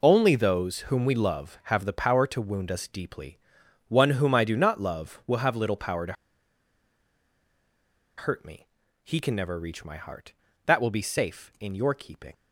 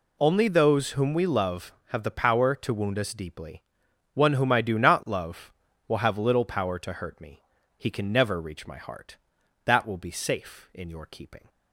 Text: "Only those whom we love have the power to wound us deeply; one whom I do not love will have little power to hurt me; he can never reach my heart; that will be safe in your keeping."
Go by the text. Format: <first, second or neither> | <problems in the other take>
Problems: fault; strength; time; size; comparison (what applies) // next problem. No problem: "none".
second | pauses between "to" and "hurt"; strong; at 6.1 s; 2.0 s long